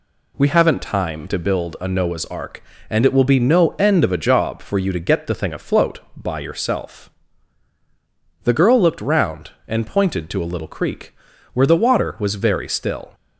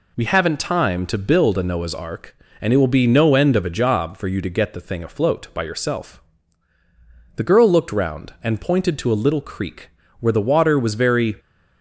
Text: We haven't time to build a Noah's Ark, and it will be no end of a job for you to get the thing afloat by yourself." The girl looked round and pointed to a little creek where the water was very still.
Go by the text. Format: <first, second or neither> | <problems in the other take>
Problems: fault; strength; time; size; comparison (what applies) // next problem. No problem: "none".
first | pauses between "creek" and "where"; slight; at 9.8 s; 0.32 s long; also in the first // stops before "still"; at 11.3 s